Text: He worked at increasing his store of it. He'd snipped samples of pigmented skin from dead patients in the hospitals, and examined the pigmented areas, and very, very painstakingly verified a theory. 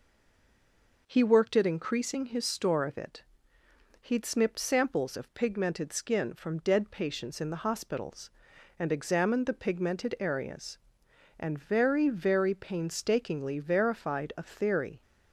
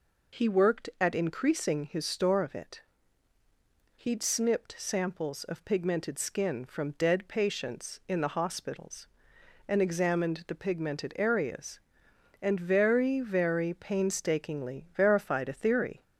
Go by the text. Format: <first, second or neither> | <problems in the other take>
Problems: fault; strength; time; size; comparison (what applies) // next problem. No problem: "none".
second | stays silent before the first word; until 1.0 s; 1.0 s long